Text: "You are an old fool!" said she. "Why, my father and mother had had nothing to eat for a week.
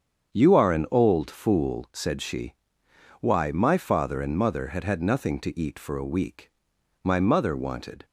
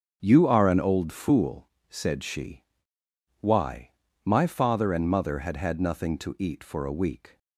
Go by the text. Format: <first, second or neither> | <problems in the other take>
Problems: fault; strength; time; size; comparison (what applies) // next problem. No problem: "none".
second | starts louder than the rest; strong; until 1.3 s; 7.5 dB; also in the second // goes on to say "My mother wanted"; noticeable; from 7.0 s on; 1.0 s long